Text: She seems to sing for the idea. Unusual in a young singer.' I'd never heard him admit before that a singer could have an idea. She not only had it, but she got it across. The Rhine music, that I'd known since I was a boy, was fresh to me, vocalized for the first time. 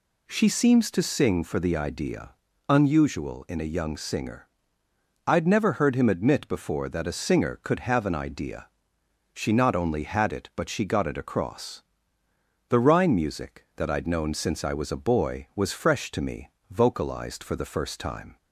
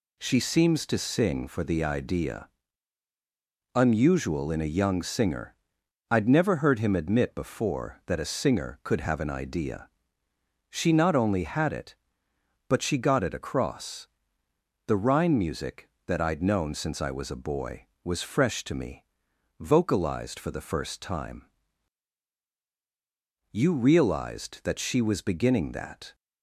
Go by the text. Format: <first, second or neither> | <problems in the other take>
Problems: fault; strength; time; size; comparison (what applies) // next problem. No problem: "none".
first | goes on to say "You realized that she was beginning that"; strong; from 23.5 s on; 2.6 s long